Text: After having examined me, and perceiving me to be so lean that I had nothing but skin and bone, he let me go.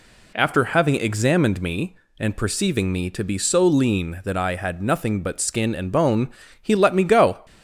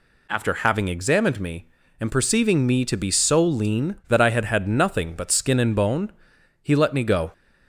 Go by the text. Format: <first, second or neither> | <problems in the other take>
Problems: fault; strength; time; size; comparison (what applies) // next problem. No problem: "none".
first | says "had" twice; at 4.4 s